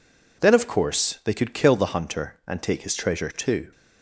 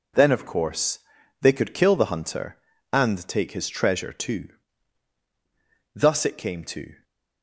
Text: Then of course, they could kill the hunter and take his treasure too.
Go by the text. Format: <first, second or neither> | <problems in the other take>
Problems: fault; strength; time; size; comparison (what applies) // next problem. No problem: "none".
first | goes on to say "Thus it came to"; noticeable; from 5.9 s on; 1.0 s long